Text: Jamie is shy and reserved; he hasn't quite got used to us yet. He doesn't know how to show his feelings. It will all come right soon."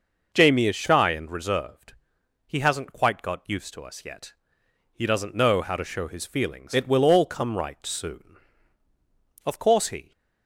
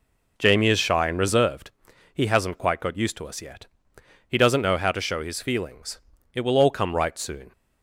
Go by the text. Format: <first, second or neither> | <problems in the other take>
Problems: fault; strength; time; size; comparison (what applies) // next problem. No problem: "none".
second | goes on to say "Of course he"; noticeable; from 9.4 s on; 0.68 s long